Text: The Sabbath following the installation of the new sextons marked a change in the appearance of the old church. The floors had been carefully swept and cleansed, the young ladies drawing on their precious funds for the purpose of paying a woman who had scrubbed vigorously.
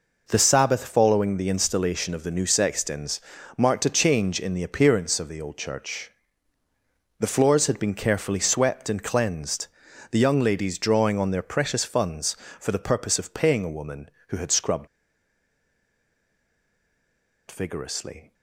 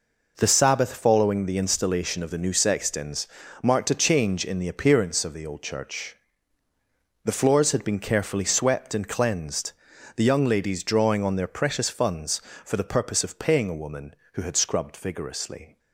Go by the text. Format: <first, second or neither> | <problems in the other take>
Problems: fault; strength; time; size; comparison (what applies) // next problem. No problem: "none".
second | pauses between "sextons" and "marked"; slight; at 3.2 s; 0.36 s long; slight in the second // pauses between "scrubbed" and "vigorously"; strong; at 14.8 s; 2.6 s long